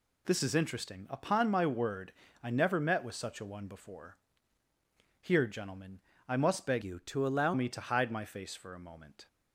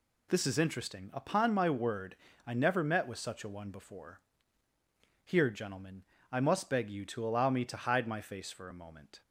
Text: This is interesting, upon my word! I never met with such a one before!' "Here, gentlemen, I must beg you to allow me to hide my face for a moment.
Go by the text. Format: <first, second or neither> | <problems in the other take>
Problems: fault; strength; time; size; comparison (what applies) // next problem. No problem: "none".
second | changes voice from "you" to "allow"; from 6.8 to 7.5 s; 0.7 s long